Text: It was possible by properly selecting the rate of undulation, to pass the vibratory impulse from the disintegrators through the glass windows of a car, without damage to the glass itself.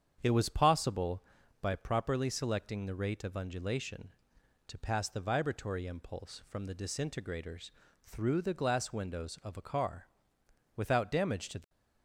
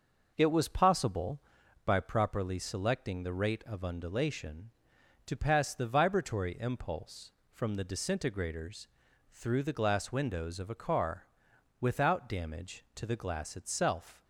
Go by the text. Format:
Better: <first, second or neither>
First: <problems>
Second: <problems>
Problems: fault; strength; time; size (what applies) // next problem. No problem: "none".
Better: second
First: starts louder than the rest; strong; until 1.2 s; 8 dB // pauses between "disintegrators" and "through"; slight; at 7.7 s; 0.34 s long // stops before "glass itself"; at 11.6 s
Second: pauses between "disintegrators" and "through"; at 8.8 s; 0.42 s long